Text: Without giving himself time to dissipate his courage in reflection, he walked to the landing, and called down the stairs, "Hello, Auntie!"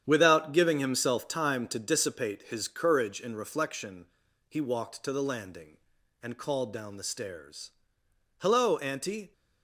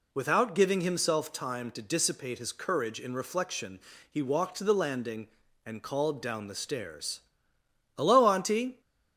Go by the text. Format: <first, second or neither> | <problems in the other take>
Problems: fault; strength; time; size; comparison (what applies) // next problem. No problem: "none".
second | gets quieter; strong; throughout; 9 dB